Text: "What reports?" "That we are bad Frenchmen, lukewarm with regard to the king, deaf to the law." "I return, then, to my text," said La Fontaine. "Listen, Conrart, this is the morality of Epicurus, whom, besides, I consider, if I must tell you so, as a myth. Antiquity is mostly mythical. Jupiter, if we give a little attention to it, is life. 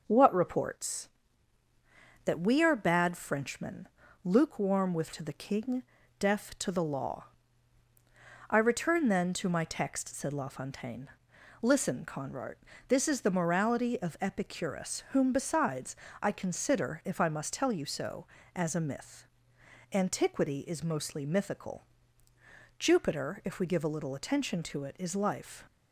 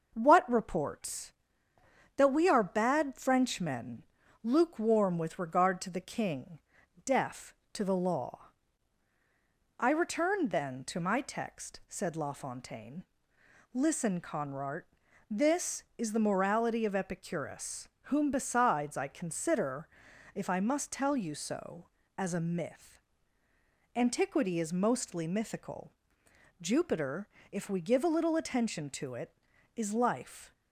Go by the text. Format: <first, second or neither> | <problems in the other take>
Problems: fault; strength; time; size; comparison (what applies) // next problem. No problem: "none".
second | skips "regard"; at 5.1 s